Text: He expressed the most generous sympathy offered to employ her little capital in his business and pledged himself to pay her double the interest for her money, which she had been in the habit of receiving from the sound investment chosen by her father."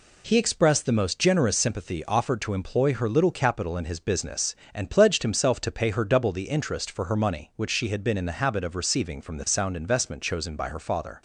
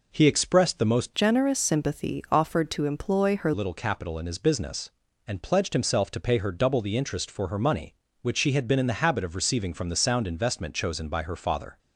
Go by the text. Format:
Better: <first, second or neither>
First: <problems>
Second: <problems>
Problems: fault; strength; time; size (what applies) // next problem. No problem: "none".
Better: first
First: none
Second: changes voice from "generous" to "her"; from 1.1 to 3.5 s; 2.4 s long